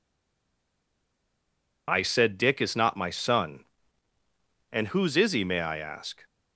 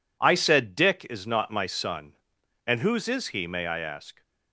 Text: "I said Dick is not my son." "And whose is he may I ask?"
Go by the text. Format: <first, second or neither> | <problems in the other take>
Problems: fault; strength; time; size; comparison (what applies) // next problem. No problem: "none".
second | stays silent before the first word; noticeable; until 1.8 s; 1.8 s long